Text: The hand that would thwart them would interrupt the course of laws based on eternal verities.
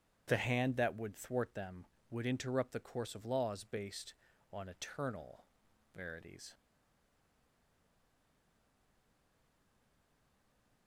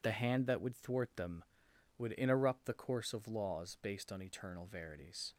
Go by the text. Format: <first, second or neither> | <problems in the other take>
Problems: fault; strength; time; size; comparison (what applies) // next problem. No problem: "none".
second | starts louder than the rest; strong; until 1.2 s; 9.5 dB // pauses between "eternal" and "verities"; noticeable; at 5.4 s; 0.50 s long // stays silent after the last word; strong; from 6.5 s on; 4.3 s long